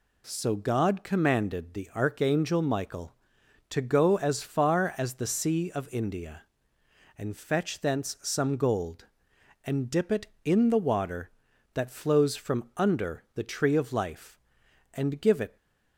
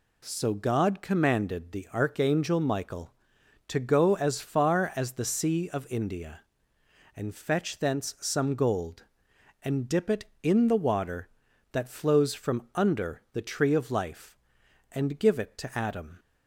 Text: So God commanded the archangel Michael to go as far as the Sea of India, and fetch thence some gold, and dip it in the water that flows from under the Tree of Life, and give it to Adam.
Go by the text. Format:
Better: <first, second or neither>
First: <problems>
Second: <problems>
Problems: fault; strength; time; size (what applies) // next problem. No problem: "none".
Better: second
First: stops before "to Adam"; at 15.5 s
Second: none